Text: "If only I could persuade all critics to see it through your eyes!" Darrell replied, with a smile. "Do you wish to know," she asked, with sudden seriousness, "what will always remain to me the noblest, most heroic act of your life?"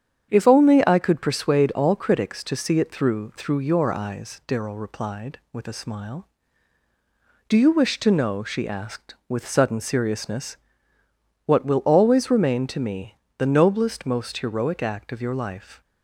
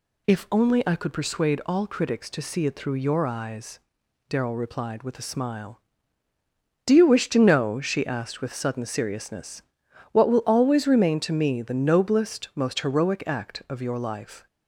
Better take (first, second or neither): second